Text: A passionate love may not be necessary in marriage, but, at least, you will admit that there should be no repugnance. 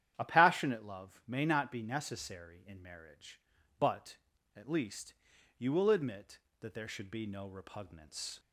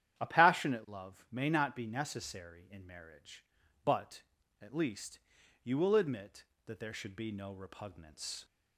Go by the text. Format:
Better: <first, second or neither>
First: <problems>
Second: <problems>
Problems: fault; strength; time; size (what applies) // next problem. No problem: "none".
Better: neither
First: starts louder than the rest; strong; until 1.1 s; 10.5 dB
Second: starts louder than the rest; strong; until 1.2 s; 10 dB